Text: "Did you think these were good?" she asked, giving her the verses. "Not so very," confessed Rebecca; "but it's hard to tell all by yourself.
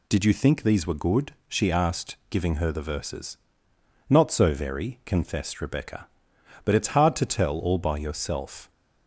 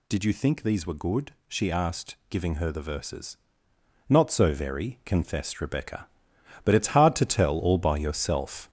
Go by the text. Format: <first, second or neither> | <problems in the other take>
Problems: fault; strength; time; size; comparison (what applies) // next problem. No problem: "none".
first | gets louder; noticeable; throughout; 5.5 dB